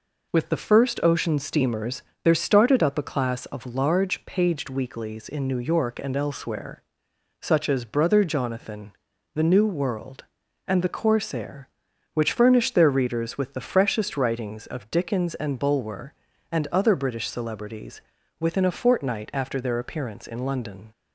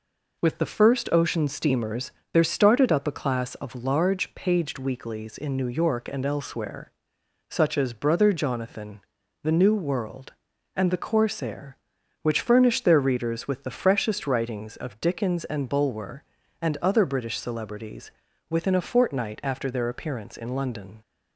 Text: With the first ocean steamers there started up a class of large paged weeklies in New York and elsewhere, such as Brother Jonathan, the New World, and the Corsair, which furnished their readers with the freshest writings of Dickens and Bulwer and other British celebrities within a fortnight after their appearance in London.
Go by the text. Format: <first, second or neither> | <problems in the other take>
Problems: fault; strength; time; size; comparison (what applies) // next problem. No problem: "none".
neither | pauses between "steamers" and "there"; slight; the same in both // pauses between "celebrities" and "within"; slight; the same in both